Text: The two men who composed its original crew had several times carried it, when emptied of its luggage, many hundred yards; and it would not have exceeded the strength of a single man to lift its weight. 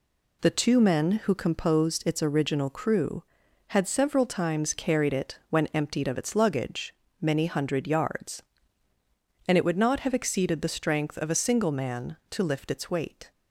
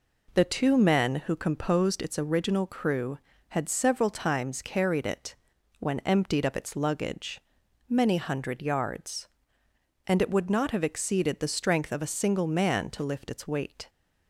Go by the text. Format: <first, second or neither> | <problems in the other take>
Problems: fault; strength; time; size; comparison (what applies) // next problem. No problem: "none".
neither | none